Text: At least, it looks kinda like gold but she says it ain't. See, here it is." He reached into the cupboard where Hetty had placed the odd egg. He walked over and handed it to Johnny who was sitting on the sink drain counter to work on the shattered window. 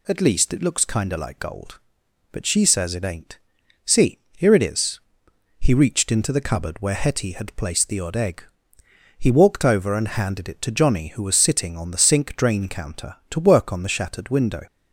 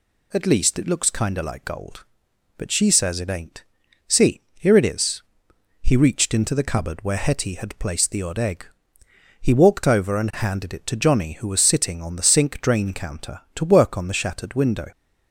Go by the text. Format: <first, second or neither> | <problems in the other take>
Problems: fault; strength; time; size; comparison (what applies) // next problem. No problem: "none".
neither | none